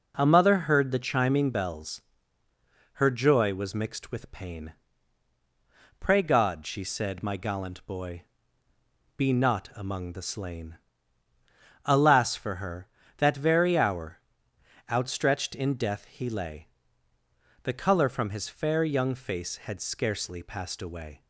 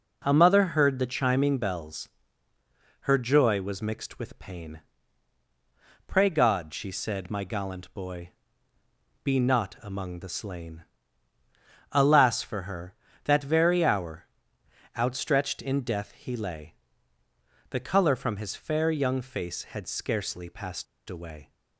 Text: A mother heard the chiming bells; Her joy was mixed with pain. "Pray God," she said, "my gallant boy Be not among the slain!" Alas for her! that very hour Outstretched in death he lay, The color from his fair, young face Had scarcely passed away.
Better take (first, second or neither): first